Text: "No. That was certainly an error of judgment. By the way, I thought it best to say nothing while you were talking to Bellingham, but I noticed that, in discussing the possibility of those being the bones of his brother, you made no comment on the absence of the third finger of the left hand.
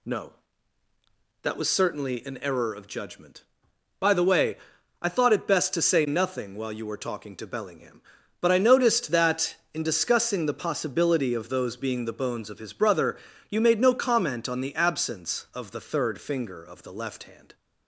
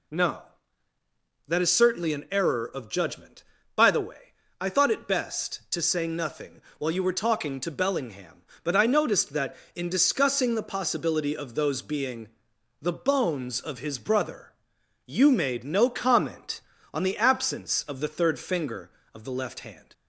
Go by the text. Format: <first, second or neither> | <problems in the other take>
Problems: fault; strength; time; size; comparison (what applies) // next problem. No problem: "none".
first | says "is" for "was"; at 1.6 s // pauses between "nothing" and "while"; slight; at 6.6 s; 0.18 s long // pauses between "being" and "the"; noticeable; at 12.2 s; 0.54 s long